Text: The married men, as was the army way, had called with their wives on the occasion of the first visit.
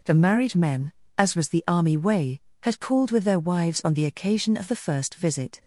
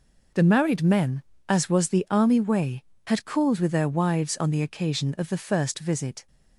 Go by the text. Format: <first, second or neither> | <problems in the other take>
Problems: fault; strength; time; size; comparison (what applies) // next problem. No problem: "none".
neither | none